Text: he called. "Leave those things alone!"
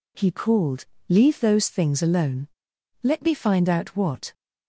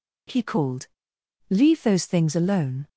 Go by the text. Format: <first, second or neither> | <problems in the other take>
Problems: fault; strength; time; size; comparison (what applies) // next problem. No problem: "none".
second | goes on to say "Let me find out what"; from 3.0 s on; 1.3 s long